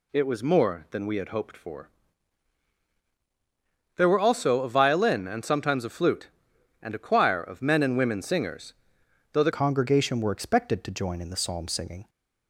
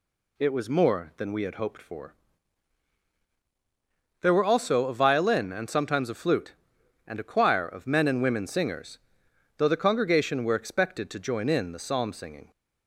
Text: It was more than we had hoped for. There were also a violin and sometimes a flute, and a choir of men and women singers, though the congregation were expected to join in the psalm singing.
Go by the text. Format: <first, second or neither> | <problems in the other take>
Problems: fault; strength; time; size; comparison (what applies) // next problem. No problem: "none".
second | changes voice at "congregation"; from 9.5 s on; 2.5 s long